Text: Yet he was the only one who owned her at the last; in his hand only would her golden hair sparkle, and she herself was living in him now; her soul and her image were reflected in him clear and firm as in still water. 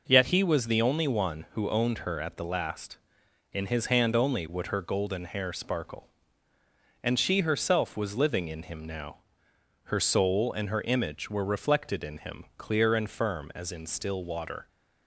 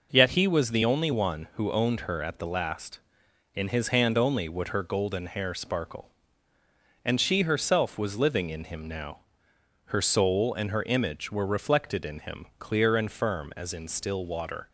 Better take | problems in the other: neither | none

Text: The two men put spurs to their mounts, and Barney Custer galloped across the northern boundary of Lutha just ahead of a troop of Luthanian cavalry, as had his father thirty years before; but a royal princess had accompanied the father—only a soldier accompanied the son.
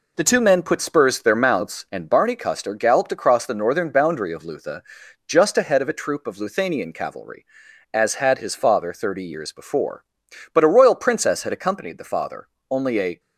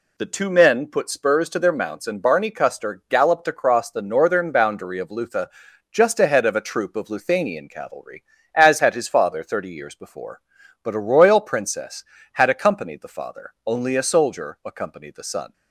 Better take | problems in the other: second | pauses between "Lutha" and "just"; noticeable; at 4.8 s; 0.46 s long; also in the second // stops before "soldier accompanied the son"; at 13.1 s

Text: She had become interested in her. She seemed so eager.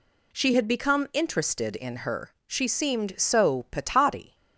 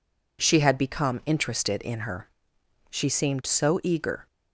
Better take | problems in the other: second | says "patati" for "eager"; at 3.7 s

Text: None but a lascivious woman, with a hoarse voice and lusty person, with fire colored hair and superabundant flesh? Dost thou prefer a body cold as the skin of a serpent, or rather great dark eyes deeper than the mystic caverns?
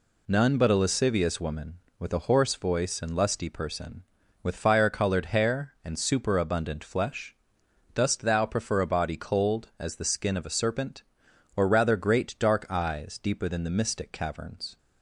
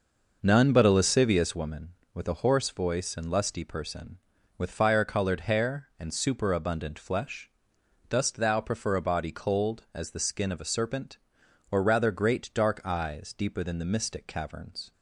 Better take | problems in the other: first | starts louder than the rest; noticeable; until 1.6 s; 5.5 dB

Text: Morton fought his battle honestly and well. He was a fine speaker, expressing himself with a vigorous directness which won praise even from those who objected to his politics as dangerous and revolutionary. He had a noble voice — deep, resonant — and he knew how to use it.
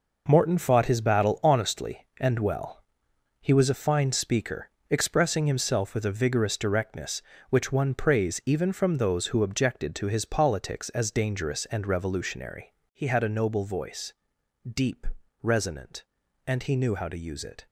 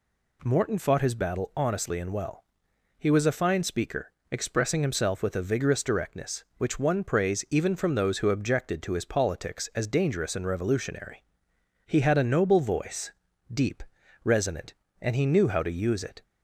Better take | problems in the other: neither | none

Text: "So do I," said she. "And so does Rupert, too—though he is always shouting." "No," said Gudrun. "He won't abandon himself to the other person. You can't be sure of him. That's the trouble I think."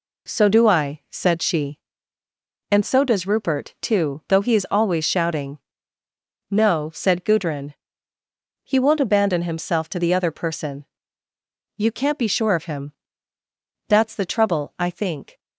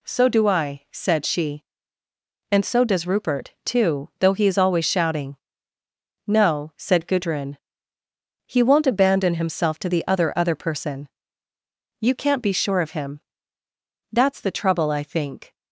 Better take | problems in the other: first | says "other" twice; at 10.3 s

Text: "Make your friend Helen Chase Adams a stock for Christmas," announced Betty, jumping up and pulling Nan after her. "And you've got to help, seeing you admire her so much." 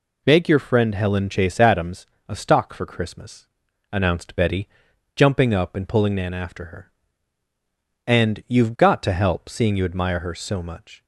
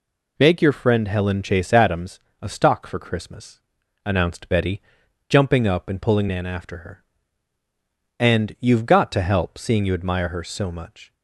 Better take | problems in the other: neither | pauses between "Adams" and "a"; slight; the same in both

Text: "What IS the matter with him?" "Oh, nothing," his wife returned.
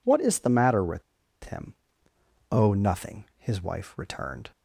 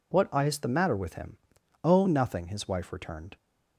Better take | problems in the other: second | pauses between "with" and "him"; at 1.0 s; 0.41 s long

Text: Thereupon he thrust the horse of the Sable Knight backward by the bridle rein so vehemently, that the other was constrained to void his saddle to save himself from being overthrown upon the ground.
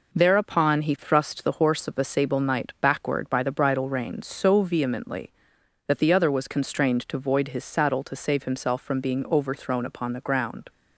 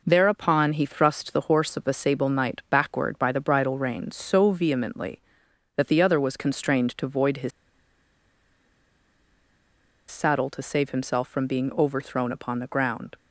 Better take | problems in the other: first | pauses between "his" and "saddle"; strong; at 7.5 s; 2.5 s long

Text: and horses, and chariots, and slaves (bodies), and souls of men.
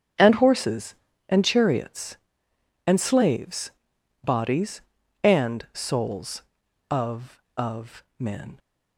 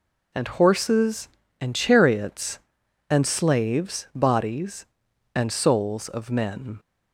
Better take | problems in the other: second | starts louder than the rest; strong; until 1.5 s; 7.5 dB // says "of" twice; at 7.5 s

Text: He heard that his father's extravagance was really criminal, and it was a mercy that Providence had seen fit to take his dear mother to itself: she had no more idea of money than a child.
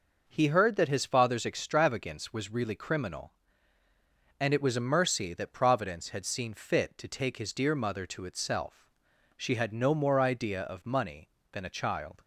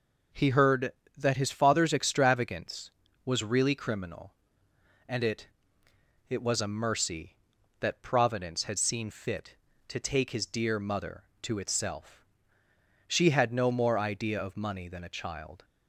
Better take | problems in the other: first | says "it" twice; at 6.3 s

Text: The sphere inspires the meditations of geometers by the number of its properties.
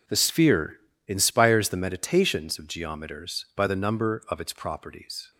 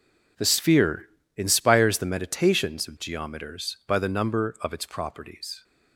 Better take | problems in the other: neither | pauses between "sphere" and "inspires"; slight; the same in both

